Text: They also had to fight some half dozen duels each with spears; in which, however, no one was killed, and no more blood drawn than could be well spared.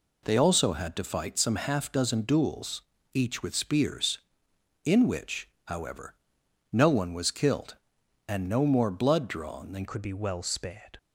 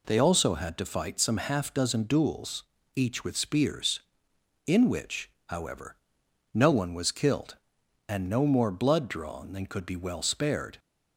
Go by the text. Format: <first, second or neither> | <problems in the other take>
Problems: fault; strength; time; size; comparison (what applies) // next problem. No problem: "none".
second | pauses between "duels" and "each"; slight; at 2.8 s; 0.30 s long; slight in the second // changes voice at "could"; from 9.8 s on; 1.1 s long